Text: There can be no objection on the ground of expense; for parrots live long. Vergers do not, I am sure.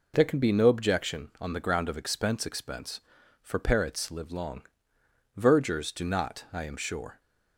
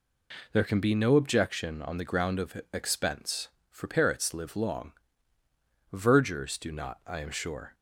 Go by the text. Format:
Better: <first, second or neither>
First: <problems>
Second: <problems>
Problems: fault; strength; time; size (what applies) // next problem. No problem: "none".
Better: second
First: says "expense" twice; at 2.4 s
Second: none